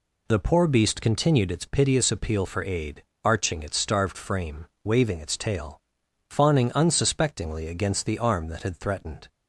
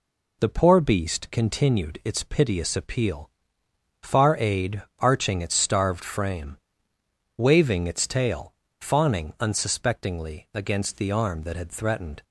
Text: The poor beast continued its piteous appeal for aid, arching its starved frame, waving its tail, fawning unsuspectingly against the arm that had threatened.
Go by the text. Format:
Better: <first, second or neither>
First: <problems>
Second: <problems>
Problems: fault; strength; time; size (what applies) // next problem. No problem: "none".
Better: first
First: none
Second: says "far" for "for"; at 4.0 s